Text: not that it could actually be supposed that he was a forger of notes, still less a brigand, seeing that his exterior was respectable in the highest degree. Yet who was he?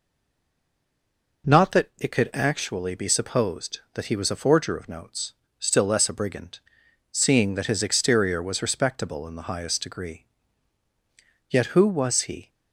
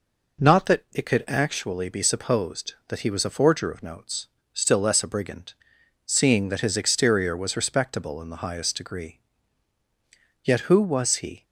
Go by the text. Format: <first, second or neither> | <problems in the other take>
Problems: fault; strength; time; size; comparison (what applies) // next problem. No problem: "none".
second | stays silent before the first word; noticeable; until 1.4 s; 1.4 s long